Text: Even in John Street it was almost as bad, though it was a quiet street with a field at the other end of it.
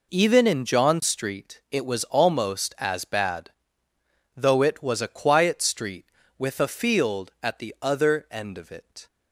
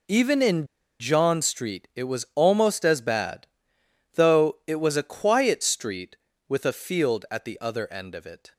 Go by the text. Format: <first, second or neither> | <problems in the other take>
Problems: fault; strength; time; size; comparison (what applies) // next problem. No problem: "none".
first | pauses between "in" and "John"; slight; at 0.6 s; 0.34 s long